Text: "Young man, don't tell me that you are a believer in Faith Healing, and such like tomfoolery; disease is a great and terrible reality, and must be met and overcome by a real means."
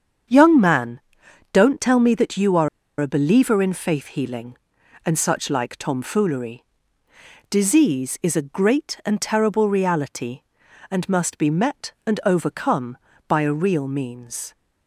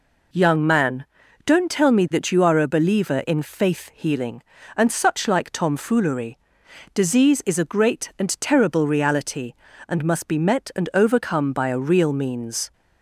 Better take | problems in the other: second | starts louder than the rest; strong; until 1.8 s; 7.5 dB // pauses between "are" and "a"; slight; at 2.6 s; 0.30 s long

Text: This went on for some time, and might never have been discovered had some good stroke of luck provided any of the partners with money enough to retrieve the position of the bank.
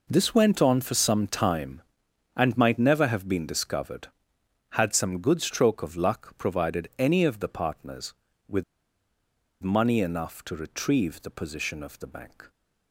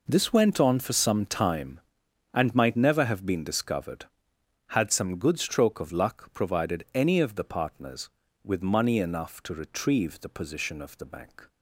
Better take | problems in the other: second | pauses between "with" and "money"; at 8.6 s; 1.0 s long

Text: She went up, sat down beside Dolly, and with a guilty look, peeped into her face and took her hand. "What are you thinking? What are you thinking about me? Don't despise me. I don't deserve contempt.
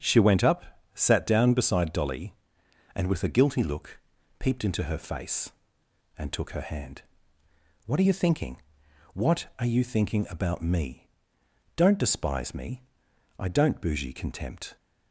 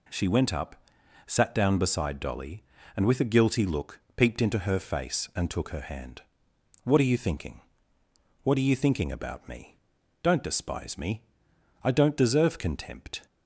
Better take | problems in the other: second | starts louder than the rest; strong; until 1.3 s; 8 dB // says "bougie" for "deserve"; at 13.8 s

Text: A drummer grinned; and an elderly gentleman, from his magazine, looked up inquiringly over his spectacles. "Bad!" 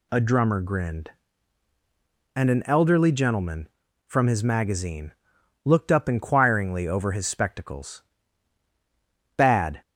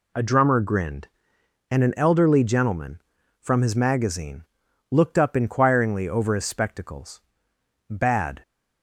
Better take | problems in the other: neither | none

